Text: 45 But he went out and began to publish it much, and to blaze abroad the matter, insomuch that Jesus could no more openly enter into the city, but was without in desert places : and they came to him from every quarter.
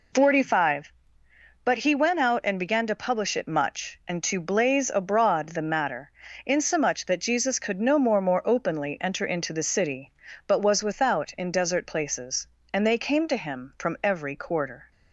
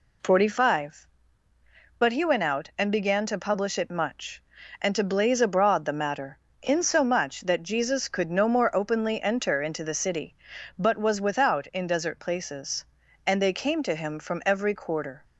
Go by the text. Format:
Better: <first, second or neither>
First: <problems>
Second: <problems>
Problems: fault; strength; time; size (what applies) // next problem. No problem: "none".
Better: second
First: says "more" twice; at 8.2 s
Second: none